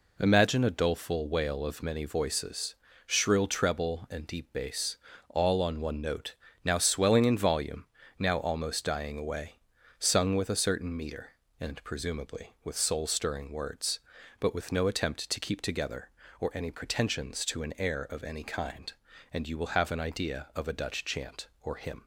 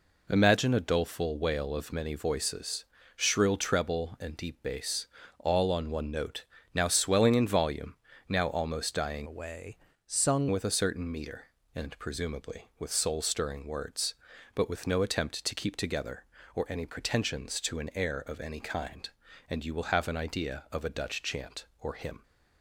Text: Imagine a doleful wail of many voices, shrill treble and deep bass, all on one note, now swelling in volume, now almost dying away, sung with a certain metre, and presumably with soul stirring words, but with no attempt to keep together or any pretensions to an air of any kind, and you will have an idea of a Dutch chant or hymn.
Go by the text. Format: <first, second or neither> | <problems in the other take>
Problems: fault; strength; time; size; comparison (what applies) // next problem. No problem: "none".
first | changes voice from "away" to "sung"; from 9.2 to 10.4 s; 1.2 s long